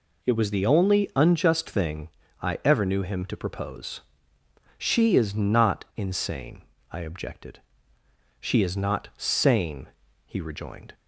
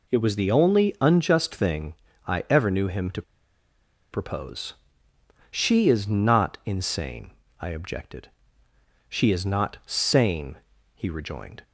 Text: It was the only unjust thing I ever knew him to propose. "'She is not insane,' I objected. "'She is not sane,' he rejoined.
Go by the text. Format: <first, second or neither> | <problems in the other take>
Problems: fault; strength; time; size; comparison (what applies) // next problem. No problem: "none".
first | pauses between "thing" and "I"; slight; at 1.9 s; 0.32 s long; slight in the first // pauses between "to" and "propose"; noticeable; at 3.2 s; 0.90 s long